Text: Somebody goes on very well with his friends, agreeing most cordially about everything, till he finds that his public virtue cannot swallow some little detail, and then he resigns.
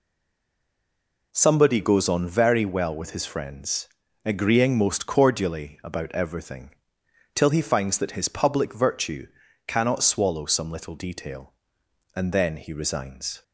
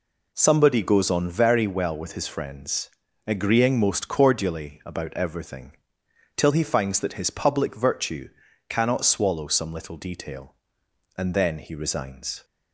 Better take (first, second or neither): second